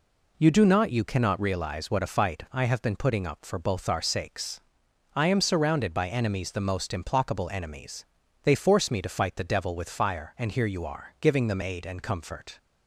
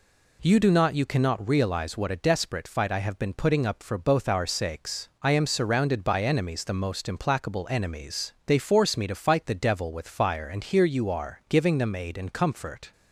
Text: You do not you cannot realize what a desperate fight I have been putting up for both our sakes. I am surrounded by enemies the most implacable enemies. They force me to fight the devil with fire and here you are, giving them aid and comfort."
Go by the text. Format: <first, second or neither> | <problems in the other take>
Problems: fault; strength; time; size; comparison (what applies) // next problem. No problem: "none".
second | skips "desperate"; at 2.0 s